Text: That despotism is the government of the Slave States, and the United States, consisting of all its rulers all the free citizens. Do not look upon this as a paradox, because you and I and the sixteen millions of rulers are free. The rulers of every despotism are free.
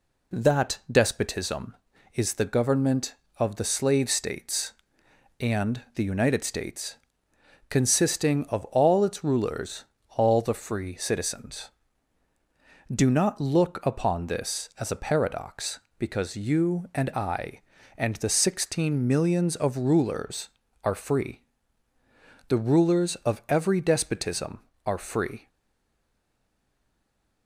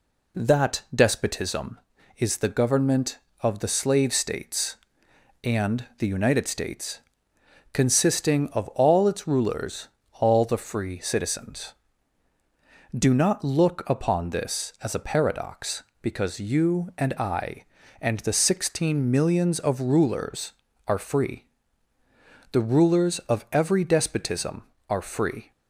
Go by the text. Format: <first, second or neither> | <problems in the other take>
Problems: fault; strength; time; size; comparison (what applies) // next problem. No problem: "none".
second | pauses between "rulers" and "all"; slight; at 9.8 s; 0.32 s long; slight in the second // stays silent after the last word; noticeable; from 25.4 s on; 2.0 s long